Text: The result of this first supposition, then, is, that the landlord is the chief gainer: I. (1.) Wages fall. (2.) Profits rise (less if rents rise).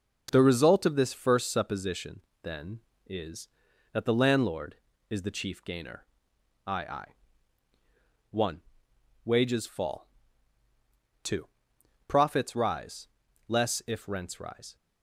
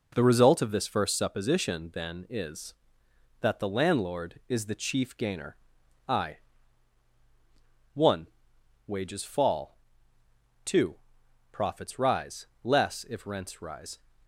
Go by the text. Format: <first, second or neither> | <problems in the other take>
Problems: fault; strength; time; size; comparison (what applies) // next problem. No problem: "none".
second | starts louder than the rest; noticeable; until 1.3 s; 6 dB // says "I" twice; at 6.8 s